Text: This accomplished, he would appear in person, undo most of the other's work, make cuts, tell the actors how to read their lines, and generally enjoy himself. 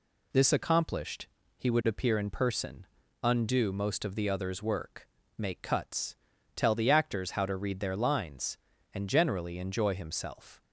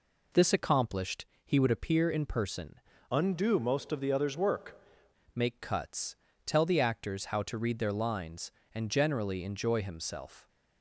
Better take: first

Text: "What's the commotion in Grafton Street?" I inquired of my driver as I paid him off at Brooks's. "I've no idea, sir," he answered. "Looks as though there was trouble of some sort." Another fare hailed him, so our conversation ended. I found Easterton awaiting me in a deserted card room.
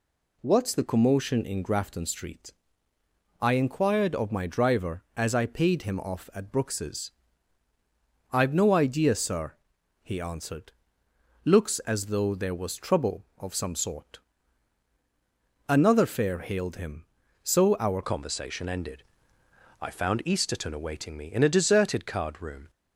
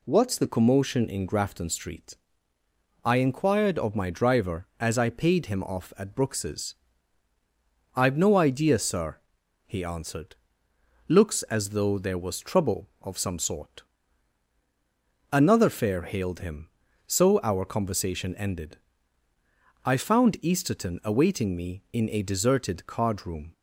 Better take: second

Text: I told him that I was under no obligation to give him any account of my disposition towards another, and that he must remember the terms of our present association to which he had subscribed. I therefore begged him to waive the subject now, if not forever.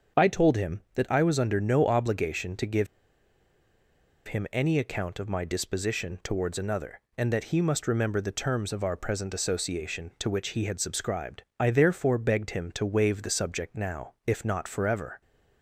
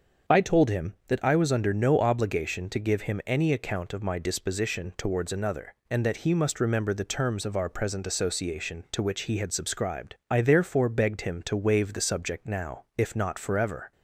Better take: second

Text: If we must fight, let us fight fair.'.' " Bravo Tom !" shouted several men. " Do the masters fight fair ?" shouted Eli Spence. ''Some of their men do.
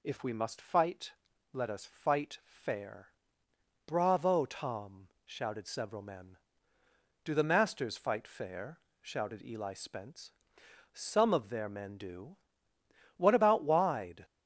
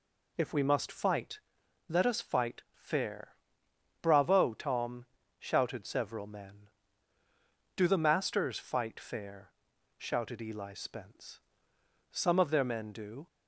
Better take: second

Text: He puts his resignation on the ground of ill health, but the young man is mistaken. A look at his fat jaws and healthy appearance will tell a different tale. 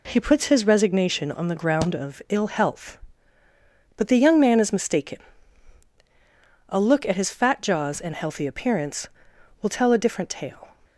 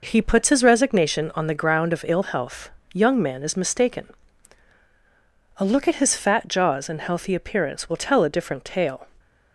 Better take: first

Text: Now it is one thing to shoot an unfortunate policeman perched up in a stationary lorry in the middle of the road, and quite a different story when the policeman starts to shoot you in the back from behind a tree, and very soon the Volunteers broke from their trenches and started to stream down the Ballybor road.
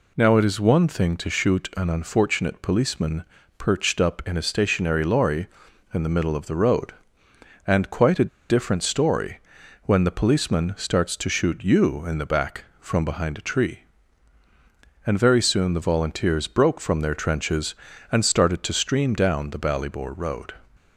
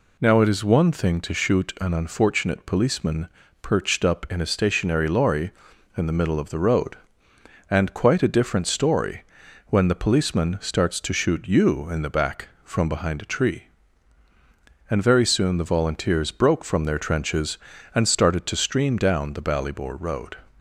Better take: second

